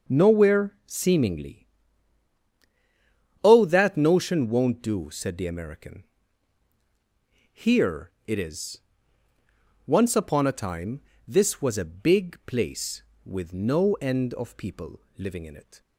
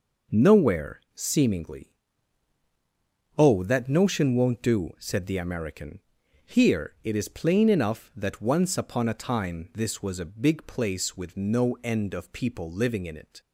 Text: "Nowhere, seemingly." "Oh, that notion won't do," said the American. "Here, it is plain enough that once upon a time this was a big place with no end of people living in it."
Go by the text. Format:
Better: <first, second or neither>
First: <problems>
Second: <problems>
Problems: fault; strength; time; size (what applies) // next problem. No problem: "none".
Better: second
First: skips "plain enough that"; at 9.3 s // pauses between "time" and "this"; slight; at 11.0 s; 0.26 s long // pauses between "people" and "living"; slight; at 15.0 s; 0.16 s long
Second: none